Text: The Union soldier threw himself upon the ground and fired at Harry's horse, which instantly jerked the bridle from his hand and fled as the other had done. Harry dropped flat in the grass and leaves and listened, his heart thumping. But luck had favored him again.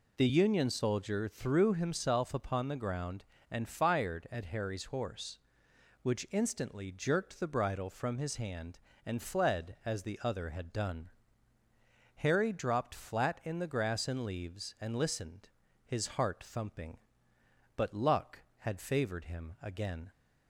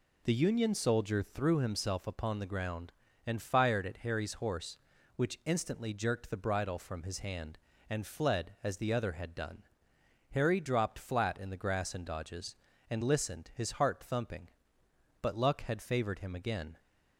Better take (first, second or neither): first